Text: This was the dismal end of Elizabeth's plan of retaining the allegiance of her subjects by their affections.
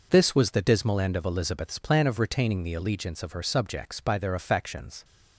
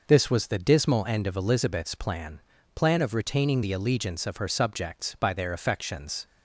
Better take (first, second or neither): first